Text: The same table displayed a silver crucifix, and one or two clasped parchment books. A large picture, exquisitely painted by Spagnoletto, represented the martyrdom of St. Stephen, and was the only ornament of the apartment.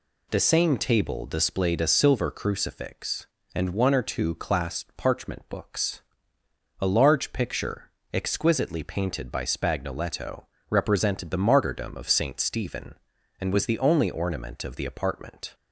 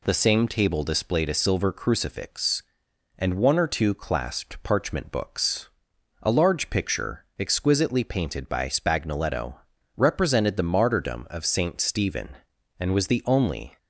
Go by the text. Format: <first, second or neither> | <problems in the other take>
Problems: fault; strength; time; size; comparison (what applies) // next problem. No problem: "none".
first | stops before "ornament of the apartment"; at 13.7 s